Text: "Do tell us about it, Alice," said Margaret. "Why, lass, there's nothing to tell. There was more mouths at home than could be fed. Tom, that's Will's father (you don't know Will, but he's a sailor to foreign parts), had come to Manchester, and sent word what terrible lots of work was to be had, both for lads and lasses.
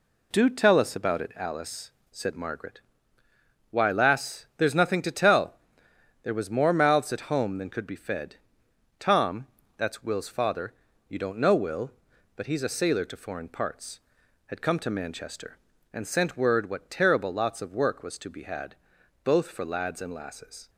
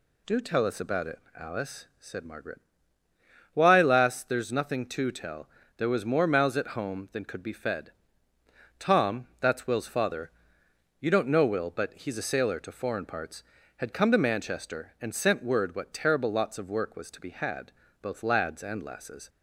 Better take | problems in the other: first | skips "for"; at 18.2 s

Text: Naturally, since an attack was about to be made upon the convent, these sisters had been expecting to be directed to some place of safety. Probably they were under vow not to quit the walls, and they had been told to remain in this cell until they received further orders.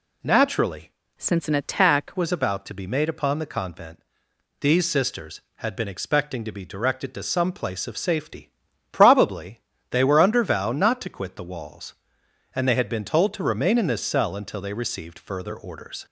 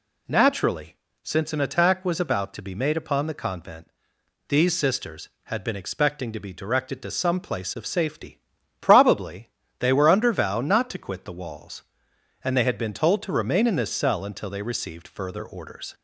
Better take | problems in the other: second | changes voice from "since" to "attack"; from 1.1 to 2.1 s; 1.0 s long // pauses between "Probably" and "they"; slight; at 9.6 s; 0.30 s long; slight in the second

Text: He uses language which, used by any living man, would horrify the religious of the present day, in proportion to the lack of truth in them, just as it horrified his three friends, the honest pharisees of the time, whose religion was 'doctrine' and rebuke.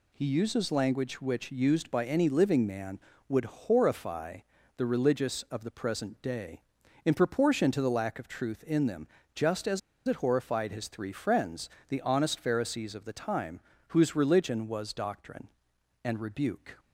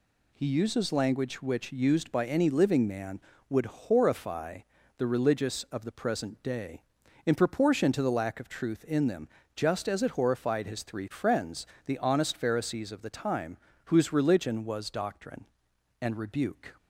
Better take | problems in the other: second | pauses between "horrify" and "the"; at 4.3 s; 0.38 s long; also in the second // pauses between "as" and "it"; slight; at 9.7 s; 0.27 s long

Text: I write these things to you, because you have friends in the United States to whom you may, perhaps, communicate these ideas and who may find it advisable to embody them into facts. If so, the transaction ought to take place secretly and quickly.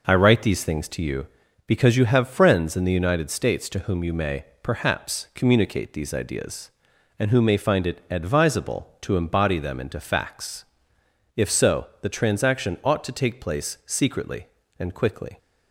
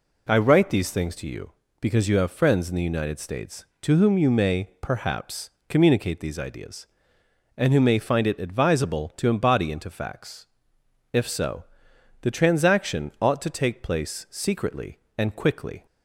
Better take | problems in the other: first | skips "them"; at 9.7 s

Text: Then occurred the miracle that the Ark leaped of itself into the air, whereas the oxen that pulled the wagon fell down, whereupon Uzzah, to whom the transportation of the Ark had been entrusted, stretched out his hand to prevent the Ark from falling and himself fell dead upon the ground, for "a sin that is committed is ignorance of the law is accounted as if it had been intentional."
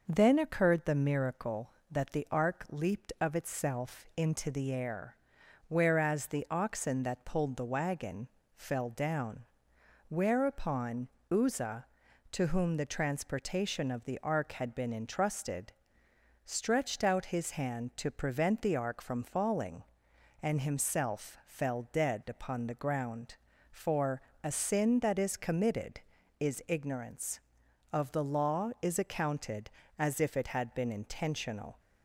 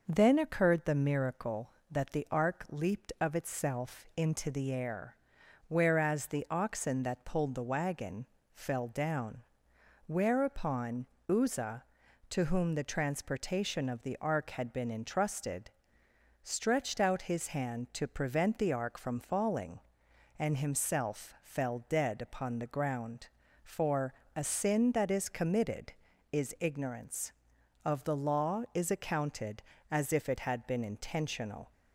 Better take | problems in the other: neither | pauses between "wagon" and "fell"; slight; the same in both // pauses between "whereupon" and "Uzzah"; slight; the same in both // pauses between "for" and "a"; slight; the same in both

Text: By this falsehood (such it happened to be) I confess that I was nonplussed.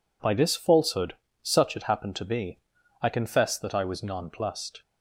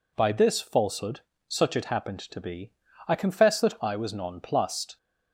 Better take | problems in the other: neither | none

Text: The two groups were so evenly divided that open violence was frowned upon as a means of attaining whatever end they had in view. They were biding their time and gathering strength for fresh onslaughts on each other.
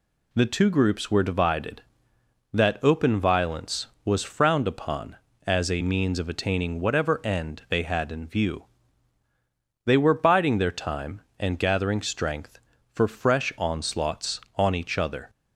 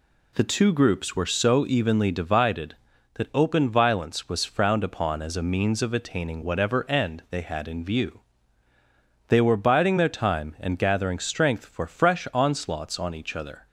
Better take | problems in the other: second | skips "so evenly"; at 1.2 s

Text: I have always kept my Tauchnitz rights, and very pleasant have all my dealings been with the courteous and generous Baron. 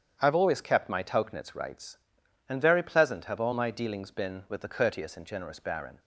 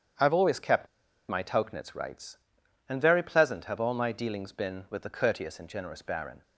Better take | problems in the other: first | starts louder than the rest; strong; until 1.6 s; 8.5 dB; strong in the first // pauses between "kept" and "my"; at 0.8 s; 0.42 s long

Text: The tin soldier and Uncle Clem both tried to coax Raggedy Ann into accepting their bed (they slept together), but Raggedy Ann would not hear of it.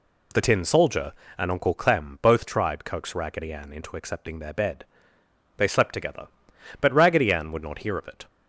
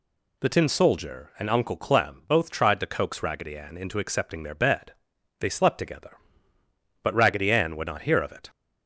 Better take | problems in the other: second | skips "to"; at 2.8 s

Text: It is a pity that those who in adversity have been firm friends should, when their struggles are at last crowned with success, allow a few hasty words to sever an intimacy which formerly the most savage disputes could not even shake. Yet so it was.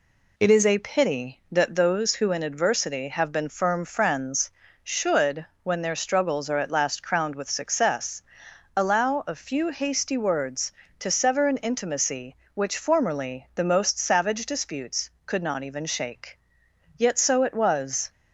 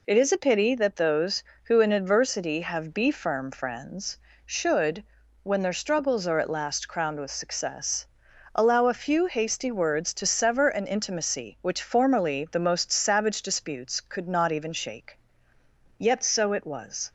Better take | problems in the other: first | says "be" for "been"; at 2.9 s

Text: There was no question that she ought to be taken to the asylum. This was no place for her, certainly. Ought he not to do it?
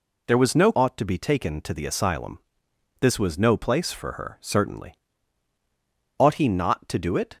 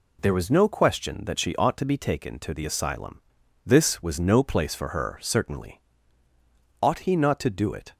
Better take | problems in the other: second | skips "question that she"; at 0.7 s

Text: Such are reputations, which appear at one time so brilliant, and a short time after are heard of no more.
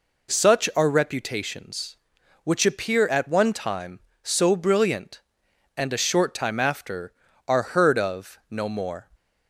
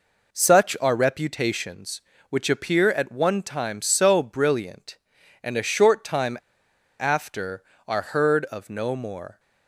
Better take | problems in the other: first | pauses between "time" and "after"; noticeable; at 6.3 s; 0.63 s long

